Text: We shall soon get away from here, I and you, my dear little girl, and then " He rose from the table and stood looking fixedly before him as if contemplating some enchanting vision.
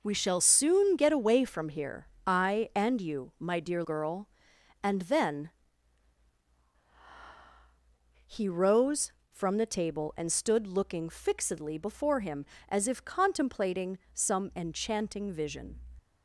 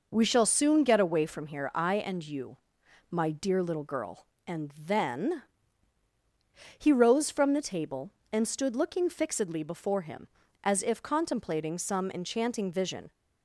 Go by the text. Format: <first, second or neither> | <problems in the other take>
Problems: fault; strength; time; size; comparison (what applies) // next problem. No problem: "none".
second | skips "little"; at 3.8 s // pauses between "contemplating" and "some"; slight; at 13.9 s; 0.16 s long